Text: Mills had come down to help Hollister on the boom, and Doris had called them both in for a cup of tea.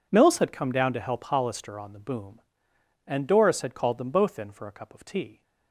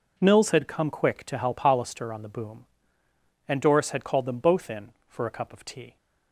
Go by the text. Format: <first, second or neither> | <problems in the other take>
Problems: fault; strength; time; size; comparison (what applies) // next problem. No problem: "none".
first | says "quick" for "down"; at 0.8 s